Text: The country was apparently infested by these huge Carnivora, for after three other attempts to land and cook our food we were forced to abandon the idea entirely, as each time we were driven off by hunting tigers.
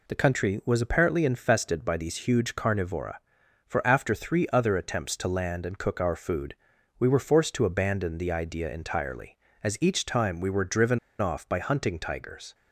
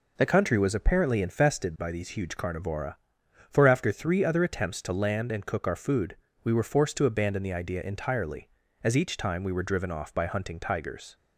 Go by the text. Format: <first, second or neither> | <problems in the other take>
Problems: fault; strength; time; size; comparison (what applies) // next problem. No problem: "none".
second | pauses between "food" and "we"; noticeable; at 6.5 s; 0.46 s long; slight in the second // pauses between "driven" and "off"; slight; at 10.9 s; 0.21 s long